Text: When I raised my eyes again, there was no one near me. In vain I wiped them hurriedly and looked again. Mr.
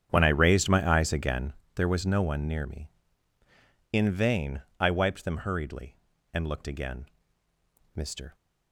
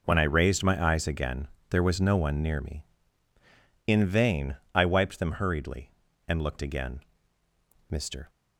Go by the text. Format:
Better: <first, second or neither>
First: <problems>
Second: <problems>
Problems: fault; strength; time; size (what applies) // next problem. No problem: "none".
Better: second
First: starts louder than the rest; strong; until 1.6 s; 9 dB // pauses between "vain" and "I"; slight; at 4.6 s; 0.20 s long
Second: pauses between "vain" and "I"; slight; at 4.5 s; 0.20 s long